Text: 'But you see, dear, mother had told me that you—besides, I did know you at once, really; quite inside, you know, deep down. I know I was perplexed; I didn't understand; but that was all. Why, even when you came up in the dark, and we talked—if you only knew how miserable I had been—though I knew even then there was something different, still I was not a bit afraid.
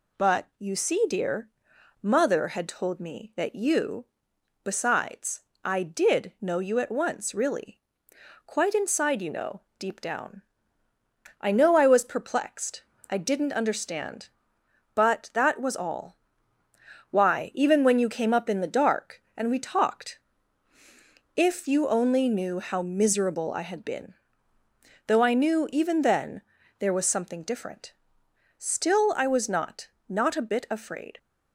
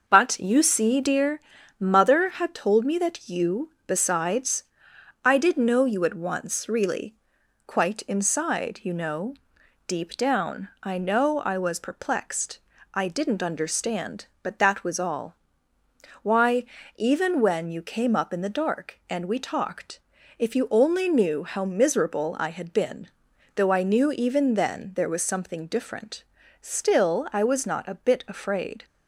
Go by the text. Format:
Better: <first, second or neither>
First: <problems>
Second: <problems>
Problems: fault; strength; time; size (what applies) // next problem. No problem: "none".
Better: second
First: pauses between "then" and "there"; slight; at 26.4 s; 0.36 s long // says "not" twice; at 30.0 s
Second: none